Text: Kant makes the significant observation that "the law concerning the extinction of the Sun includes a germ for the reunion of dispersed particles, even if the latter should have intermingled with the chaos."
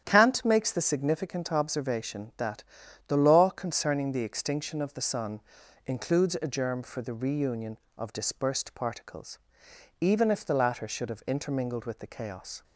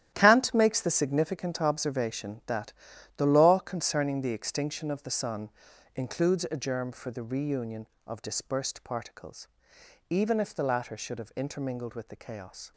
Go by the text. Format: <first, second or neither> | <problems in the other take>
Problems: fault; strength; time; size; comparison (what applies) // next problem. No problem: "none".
first | gets quieter; strong; throughout; 12 dB // starts louder than the rest; strong; until 1.1 s; 12 dB; strong in the first // pauses between "that" and "the"; at 2.7 s; 0.44 s long; also in the first // pauses between "Sun" and "includes"; at 5.5 s; 0.44 s long; also in the first